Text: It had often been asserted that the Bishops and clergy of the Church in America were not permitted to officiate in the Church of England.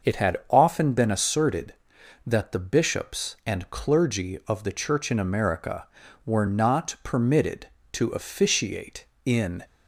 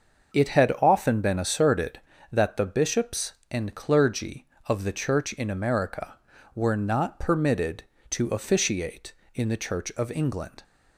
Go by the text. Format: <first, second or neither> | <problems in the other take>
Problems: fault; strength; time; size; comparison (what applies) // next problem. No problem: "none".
second | starts louder than the rest; noticeable; until 1.1 s; 6 dB; also in the second // stops before "the Church of England"; at 9.6 s